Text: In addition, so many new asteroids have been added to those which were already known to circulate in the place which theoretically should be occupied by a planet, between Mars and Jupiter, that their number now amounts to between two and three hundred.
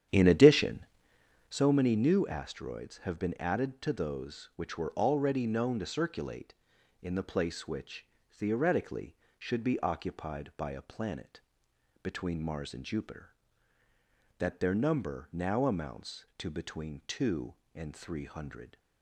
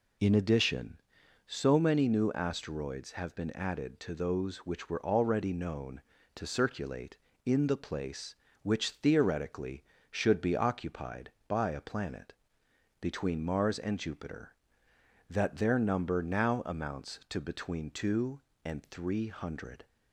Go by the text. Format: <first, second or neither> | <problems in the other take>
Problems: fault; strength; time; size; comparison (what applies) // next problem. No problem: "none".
second | starts louder than the rest; strong; until 1.7 s; 9.5 dB // pauses between "which" and "theoretically"; slight; at 8.0 s; 0.24 s long